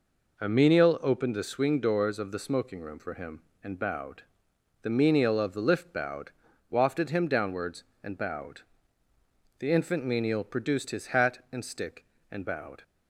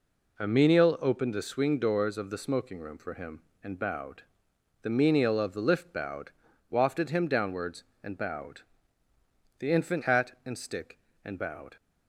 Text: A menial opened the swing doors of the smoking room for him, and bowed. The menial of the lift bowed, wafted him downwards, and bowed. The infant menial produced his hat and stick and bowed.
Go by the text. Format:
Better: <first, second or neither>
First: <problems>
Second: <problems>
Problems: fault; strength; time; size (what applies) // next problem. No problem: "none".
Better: first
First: none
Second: skips "menial produced his"; at 10.0 s